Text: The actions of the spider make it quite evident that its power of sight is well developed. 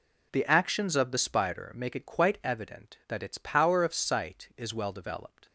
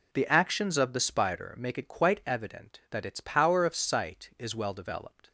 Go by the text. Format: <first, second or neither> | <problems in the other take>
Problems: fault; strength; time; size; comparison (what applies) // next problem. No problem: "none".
neither | none